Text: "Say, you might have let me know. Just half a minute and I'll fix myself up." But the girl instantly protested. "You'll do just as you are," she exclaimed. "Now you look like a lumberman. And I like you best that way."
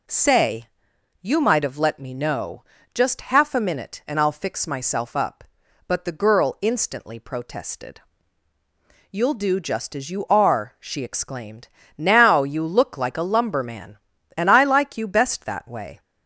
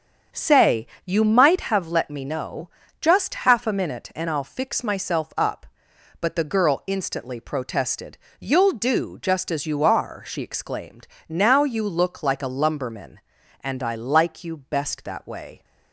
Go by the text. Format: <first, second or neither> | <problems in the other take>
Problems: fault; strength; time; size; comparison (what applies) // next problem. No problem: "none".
first | starts louder than the rest; strong; until 1.8 s; 7.5 dB